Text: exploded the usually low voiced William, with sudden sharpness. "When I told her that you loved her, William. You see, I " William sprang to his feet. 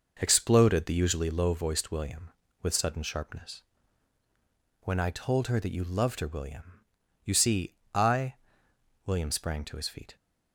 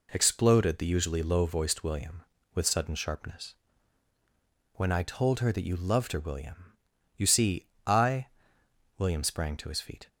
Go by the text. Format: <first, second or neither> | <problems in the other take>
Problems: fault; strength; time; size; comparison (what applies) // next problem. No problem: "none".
second | starts louder than the rest; noticeable; until 1.3 s; 6 dB